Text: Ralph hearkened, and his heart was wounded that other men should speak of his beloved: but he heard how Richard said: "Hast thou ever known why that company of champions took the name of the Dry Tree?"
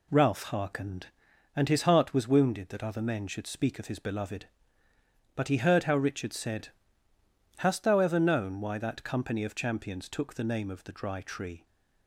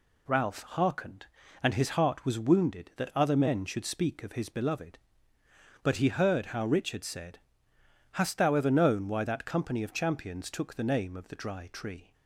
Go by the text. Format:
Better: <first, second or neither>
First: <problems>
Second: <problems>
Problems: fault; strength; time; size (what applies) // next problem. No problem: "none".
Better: neither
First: none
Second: none